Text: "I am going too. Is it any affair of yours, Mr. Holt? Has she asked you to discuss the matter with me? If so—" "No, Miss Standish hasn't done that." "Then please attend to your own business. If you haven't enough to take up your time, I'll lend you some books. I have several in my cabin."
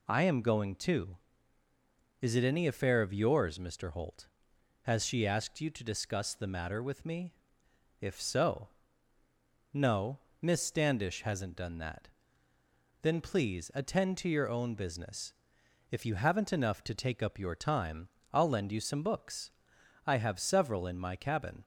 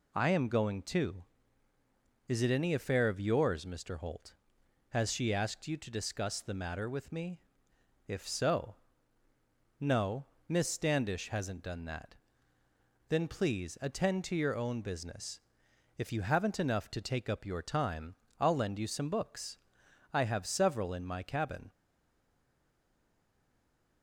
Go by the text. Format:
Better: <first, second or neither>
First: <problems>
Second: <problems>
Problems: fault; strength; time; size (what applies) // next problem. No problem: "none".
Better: first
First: none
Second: stays silent after the last word; from 21.7 s on; 2.3 s long